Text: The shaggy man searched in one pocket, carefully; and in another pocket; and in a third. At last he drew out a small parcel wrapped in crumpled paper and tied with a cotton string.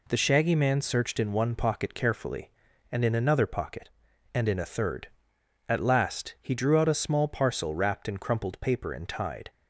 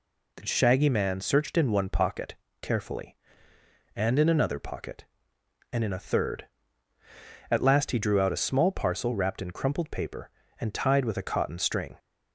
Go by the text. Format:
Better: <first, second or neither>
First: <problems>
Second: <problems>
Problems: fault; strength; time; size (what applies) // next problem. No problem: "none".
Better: second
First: stops before "with a cotton string"; at 9.4 s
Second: none